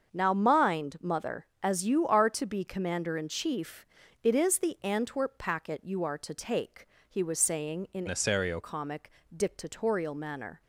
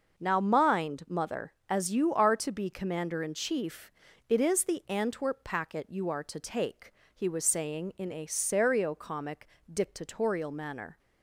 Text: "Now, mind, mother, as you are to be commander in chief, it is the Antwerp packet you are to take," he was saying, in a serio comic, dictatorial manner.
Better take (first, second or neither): second